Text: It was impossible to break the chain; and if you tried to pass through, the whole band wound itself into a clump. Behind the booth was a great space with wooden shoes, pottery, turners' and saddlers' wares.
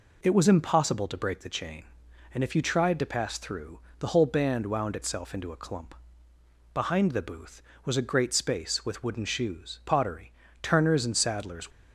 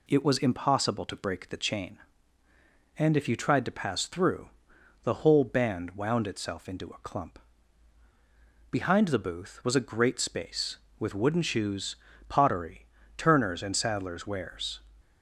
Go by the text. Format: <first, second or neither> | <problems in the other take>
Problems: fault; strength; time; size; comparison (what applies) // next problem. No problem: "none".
second | stops before "wares"; at 11.7 s